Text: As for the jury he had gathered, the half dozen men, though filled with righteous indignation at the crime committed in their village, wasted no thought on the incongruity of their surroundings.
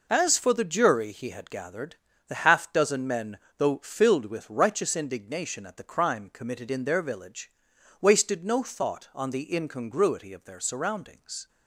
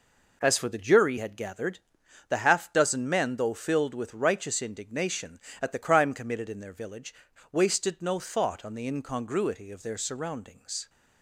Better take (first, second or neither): first